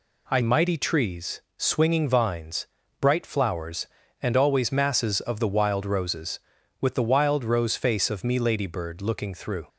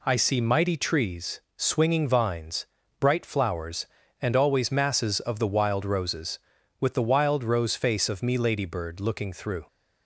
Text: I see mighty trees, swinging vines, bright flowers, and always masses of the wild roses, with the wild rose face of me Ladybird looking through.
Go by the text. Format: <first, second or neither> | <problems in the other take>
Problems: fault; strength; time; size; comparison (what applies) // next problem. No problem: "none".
second | skips "see"; at 0.4 s